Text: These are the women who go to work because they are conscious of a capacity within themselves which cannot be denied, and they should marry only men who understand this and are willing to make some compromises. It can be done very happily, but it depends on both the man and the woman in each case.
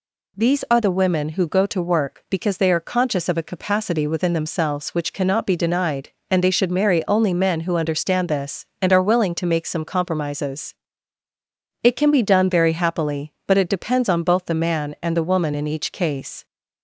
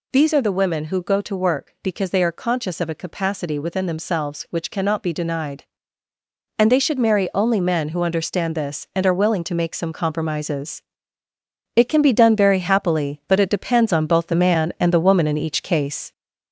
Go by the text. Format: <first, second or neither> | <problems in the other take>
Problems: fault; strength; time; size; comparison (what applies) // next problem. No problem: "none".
first | gets louder; noticeable; throughout; 4 dB